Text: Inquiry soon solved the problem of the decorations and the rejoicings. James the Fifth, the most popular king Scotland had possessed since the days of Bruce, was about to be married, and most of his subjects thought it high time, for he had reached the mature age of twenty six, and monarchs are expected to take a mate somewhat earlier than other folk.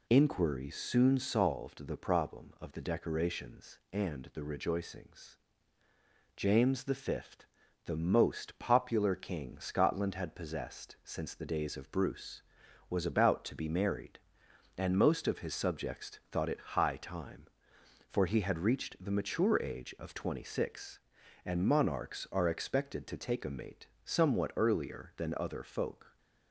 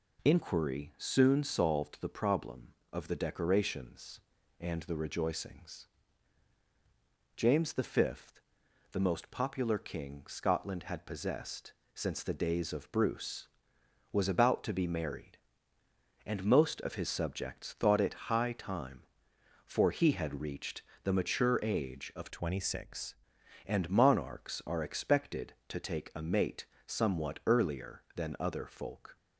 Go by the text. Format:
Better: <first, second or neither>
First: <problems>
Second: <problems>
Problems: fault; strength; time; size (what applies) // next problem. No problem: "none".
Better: first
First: pauses between "mate" and "somewhat"; slight; at 23.8 s; 0.16 s long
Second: pauses between "possessed" and "since"; slight; at 11.7 s; 0.22 s long // pauses between "reached" and "the"; slight; at 20.8 s; 0.20 s long // changes voice from "twenty" to "six"; from 22.2 to 23.1 s; 0.9 s long // pauses between "mate" and "somewhat"; slight; at 26.6 s; 0.18 s long